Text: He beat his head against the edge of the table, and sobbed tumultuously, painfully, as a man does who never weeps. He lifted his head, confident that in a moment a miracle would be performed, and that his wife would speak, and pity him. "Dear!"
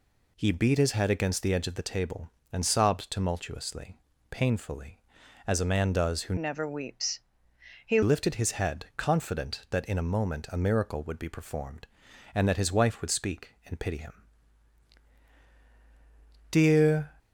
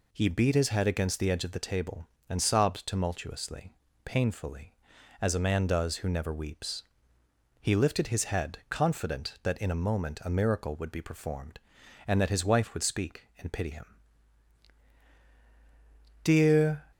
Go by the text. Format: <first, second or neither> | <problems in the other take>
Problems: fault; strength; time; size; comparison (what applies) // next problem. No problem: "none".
second | changes voice from "never" to "He"; from 6.3 to 8.0 s; 1.7 s long